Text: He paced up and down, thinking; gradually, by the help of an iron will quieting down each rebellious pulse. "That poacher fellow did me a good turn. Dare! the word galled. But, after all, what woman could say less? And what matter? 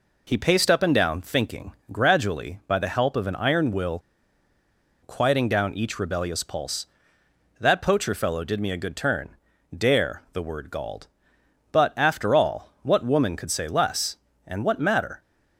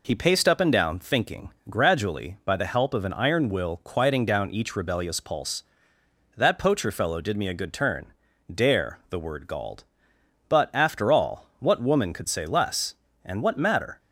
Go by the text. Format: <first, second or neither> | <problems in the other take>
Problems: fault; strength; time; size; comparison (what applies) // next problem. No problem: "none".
second | pauses between "will" and "quieting"; at 3.9 s; 1.0 s long